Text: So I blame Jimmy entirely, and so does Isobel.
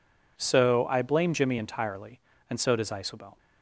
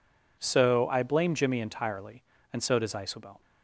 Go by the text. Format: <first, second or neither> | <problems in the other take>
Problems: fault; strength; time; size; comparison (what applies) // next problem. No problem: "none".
neither | none